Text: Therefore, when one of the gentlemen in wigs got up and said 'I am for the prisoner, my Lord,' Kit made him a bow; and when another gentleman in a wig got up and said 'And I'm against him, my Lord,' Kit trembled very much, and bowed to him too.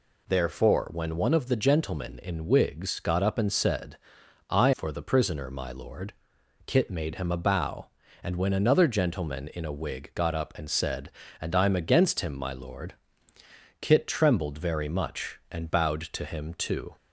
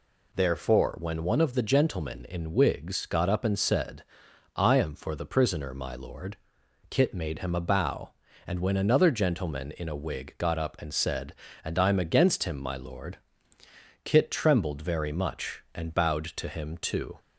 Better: second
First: pauses between "said" and "I"; noticeable; at 3.9 s; 0.52 s long // skips "am"; at 4.7 s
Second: pauses between "said" and "I"; noticeable; at 4.0 s; 0.52 s long

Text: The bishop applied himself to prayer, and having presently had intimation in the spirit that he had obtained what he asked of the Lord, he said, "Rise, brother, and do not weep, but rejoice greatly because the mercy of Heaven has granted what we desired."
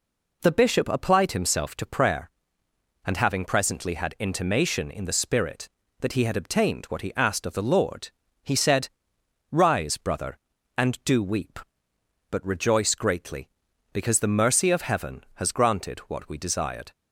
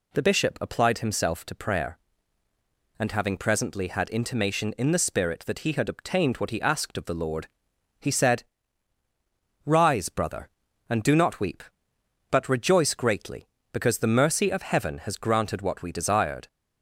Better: second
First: skips "not"; at 11.2 s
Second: none

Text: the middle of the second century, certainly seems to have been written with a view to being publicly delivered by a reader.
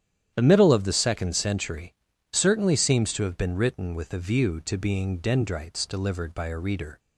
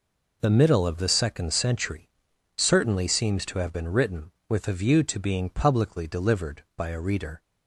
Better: second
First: starts louder than the rest; strong; until 1.3 s; 10 dB // says "dendrites" for "publicly"; at 5.1 s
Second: none

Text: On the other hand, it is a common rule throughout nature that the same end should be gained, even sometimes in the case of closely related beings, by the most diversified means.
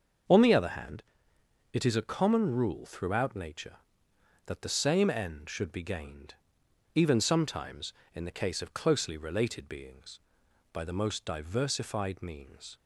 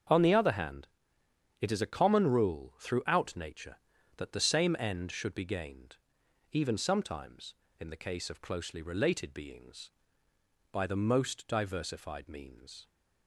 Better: neither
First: starts louder than the rest; until 1.9 s; 6.5 dB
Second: starts louder than the rest; until 1.8 s; 7 dB

